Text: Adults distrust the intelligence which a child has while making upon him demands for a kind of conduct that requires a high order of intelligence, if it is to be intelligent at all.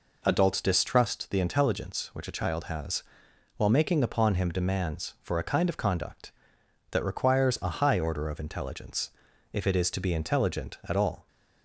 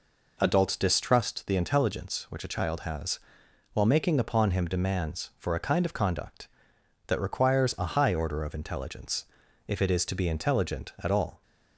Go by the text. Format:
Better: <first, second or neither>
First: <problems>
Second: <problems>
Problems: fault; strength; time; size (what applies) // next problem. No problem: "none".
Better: neither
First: pauses between "has" and "while"; noticeable; at 3.0 s; 0.54 s long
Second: pauses between "has" and "while"; noticeable; at 3.1 s; 0.54 s long